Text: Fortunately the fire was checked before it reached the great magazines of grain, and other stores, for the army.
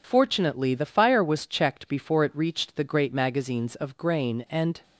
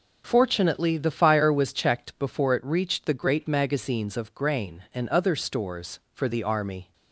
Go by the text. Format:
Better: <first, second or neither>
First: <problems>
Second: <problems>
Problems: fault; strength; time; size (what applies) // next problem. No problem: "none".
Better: second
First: stops before "other stores for the army"; at 4.8 s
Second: none